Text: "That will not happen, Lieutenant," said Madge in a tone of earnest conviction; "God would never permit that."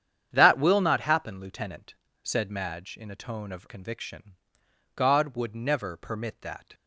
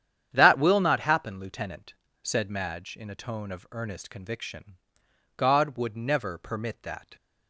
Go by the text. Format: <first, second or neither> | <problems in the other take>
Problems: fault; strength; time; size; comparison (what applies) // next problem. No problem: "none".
second | starts louder than the rest; strong; until 1.3 s; 8.5 dB; strong in the second // skips "earnest"; at 3.6 s